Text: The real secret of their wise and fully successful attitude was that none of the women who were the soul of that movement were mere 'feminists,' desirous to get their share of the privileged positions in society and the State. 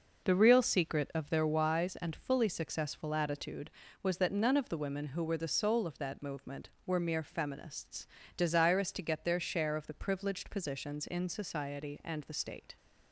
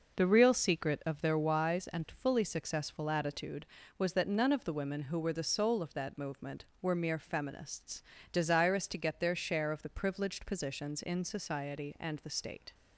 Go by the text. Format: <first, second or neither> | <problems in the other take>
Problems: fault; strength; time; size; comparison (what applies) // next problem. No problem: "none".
neither | none